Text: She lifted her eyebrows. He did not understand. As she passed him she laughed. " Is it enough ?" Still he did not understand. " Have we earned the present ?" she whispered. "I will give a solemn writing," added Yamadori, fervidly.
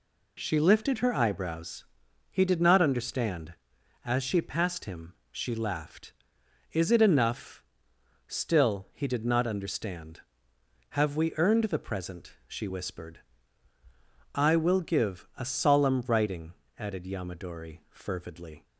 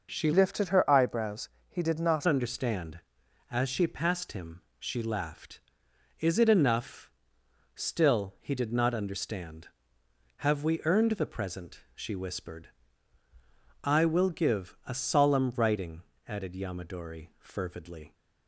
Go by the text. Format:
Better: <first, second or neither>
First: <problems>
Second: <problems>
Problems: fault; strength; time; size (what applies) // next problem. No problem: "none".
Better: first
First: pauses between "him" and "she"; slight; at 5.1 s; 0.18 s long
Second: starts louder than the rest; until 1.1 s; 6.5 dB // changes voice from "lifted" to "not"; from 0.3 to 2.2 s; 1.9 s long // pauses between "him" and "she"; slight; at 4.6 s; 0.18 s long